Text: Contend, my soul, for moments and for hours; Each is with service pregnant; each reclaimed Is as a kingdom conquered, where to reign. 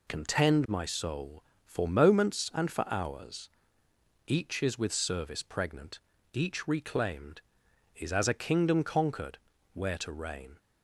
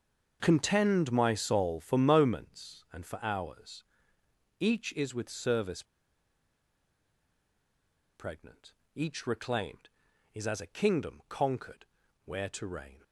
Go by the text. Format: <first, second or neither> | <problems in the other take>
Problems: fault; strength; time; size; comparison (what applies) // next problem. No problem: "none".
first | starts louder than the rest; until 1.4 s; 6.5 dB // pauses between "service" and "pregnant"; strong; at 5.8 s; 2.3 s long